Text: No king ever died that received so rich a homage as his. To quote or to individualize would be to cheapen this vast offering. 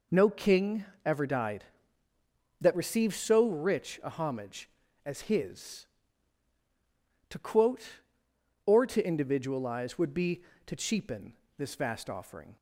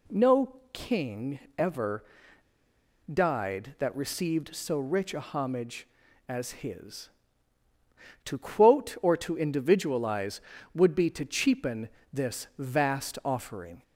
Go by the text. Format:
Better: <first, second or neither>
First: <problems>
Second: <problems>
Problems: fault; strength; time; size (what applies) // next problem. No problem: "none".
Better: first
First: pauses between "king" and "ever"; slight; at 0.8 s; 0.20 s long // pauses between "cheapen" and "this"; slight; at 11.3 s; 0.24 s long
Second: pauses between "No" and "king"; slight; at 0.5 s; 0.20 s long // pauses between "king" and "ever"; slight; at 1.3 s; 0.20 s long // pauses between "ever" and "died"; at 2.0 s; 1.0 s long // pauses between "cheapen" and "this"; slight; at 11.8 s; 0.24 s long